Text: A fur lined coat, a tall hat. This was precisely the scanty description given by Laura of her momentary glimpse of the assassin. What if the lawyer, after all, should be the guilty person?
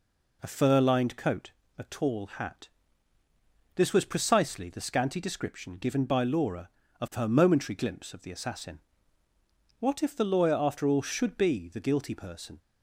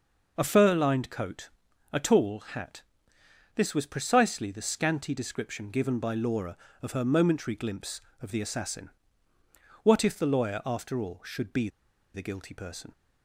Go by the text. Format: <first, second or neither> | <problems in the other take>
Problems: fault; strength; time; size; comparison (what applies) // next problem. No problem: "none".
first | pauses between "be" and "the"; noticeable; at 11.6 s; 0.46 s long